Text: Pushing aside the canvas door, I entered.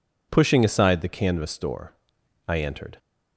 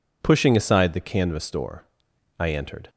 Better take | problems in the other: neither | none

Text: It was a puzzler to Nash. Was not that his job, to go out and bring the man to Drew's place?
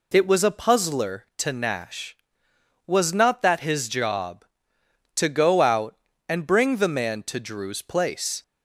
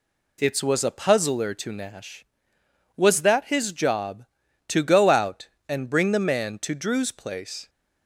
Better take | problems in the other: first | skips "not"; at 3.2 s

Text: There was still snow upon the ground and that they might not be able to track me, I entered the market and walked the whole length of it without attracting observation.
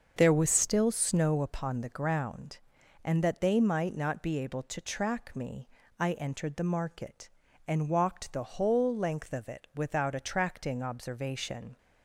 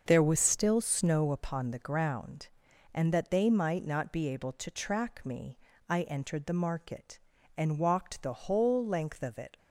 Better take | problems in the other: first | starts louder than the rest; until 1.0 s; 6.5 dB; also in the first // stops before "without attracting observation"; at 9.5 s

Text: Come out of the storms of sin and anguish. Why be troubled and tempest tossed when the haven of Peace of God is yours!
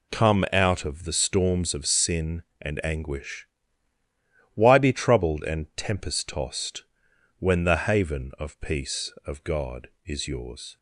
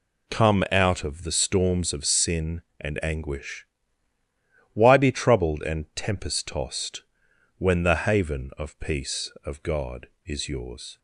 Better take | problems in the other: neither | pauses between "tossed" and "when"; noticeable; the same in both

